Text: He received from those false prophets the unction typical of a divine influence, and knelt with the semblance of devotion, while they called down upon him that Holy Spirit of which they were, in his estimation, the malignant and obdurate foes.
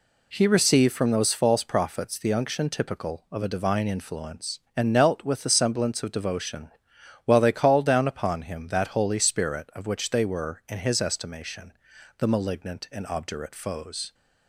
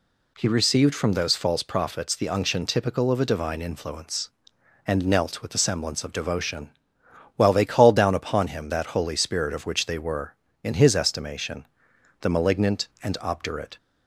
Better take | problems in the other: first | stops before "foes"; at 13.7 s

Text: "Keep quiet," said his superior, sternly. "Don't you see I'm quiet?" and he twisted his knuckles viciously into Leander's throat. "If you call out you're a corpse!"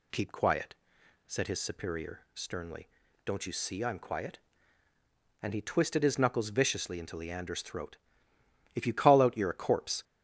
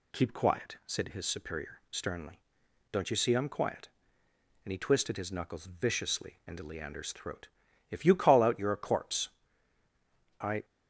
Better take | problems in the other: first | goes on to say "I"; slight; from 10.4 s on; 0.24 s long

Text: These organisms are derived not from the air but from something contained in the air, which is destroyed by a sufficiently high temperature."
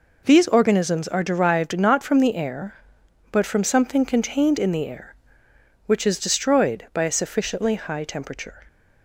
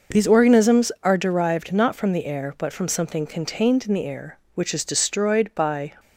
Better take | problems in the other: first | stops before "a sufficiently high temperature"; at 5.9 s

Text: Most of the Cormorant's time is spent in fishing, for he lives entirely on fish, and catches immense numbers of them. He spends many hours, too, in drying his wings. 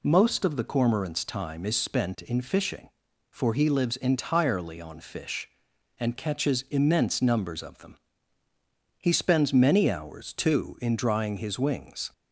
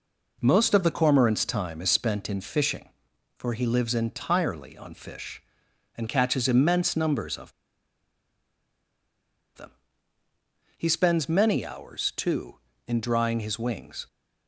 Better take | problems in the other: first | pauses between "of" and "them"; strong; at 7.5 s; 2.0 s long

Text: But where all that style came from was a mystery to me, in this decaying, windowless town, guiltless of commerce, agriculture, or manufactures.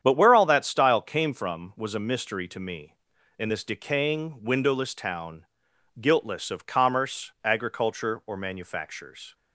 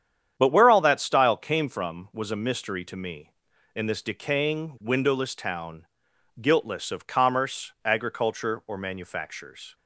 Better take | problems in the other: neither | starts louder than the rest; strong; the same in both

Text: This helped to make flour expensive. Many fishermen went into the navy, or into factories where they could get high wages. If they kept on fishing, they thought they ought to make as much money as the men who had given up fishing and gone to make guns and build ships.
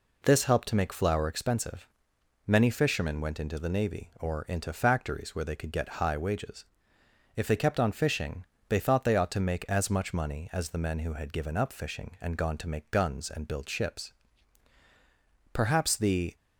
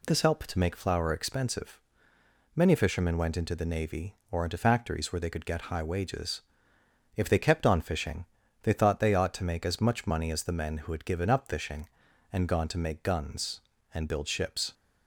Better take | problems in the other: second | goes on to say "Perhaps the"; noticeable; from 15.5 s on; 0.82 s long

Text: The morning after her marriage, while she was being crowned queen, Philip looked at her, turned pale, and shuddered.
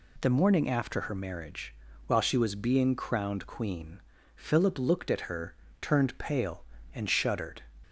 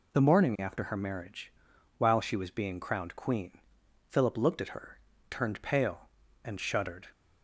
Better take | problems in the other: neither | none

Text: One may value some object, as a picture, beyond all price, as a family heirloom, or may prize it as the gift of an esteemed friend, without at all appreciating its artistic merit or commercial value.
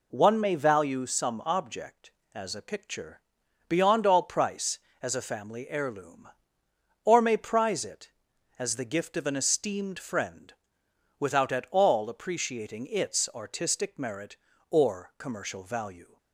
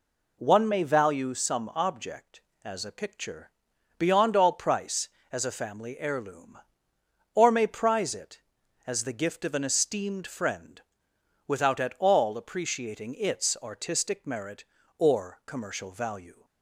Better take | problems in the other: neither | none

